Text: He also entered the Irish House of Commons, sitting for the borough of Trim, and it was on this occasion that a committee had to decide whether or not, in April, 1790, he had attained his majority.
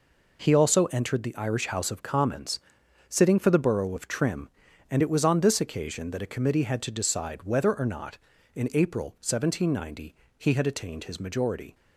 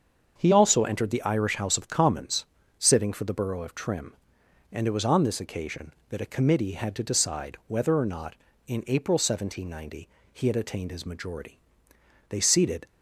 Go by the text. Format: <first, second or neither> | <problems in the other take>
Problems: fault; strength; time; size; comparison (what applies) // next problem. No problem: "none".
first | starts louder than the rest; until 1.3 s; 7 dB // goes on to say "They seated"; from 12.2 s on; 0.58 s long